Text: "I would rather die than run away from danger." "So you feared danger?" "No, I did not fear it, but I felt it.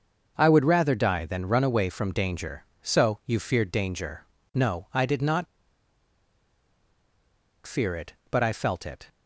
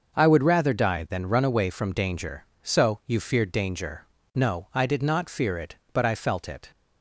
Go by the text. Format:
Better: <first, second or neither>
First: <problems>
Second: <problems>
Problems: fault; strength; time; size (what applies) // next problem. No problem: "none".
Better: second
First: starts louder than the rest; noticeable; until 1.3 s; 6 dB // pauses between "not" and "fear"; strong; at 5.4 s; 2.2 s long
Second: starts louder than the rest; until 1.2 s; 6 dB